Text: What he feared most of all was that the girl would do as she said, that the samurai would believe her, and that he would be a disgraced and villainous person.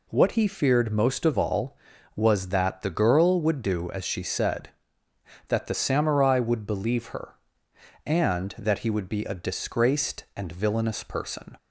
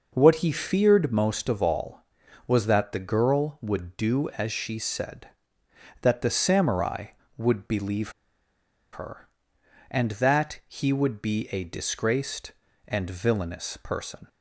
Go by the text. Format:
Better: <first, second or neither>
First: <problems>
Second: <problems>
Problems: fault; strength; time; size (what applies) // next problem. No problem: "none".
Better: first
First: none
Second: pauses between "believe" and "her"; noticeable; at 8.0 s; 0.83 s long